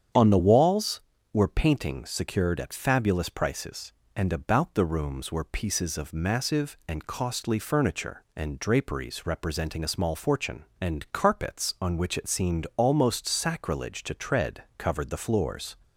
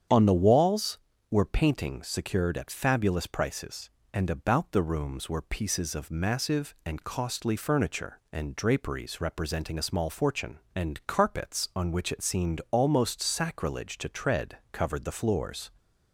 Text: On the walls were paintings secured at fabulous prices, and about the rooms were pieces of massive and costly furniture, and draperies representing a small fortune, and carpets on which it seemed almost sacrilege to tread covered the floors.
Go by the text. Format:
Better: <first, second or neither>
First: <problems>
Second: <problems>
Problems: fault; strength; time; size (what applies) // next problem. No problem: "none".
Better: neither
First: starts louder than the rest; strong; until 1.4 s; 8.5 dB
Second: starts louder than the rest; strong; until 1.4 s; 8.5 dB